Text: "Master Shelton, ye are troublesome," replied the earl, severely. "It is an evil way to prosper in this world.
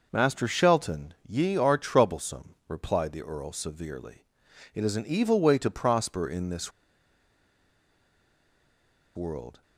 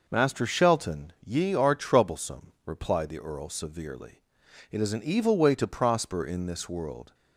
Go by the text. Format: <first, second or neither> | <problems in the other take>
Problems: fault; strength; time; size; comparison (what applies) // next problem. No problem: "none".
second | pauses between "this" and "world"; strong; at 6.7 s; 2.4 s long